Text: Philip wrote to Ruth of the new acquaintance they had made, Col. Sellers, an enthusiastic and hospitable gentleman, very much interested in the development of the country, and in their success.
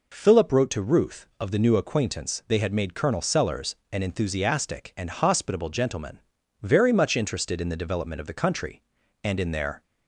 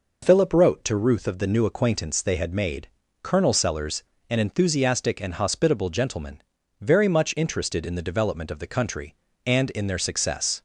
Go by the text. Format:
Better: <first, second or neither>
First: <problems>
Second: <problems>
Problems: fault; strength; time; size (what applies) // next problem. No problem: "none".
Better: second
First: stops before "success"; at 9.8 s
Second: none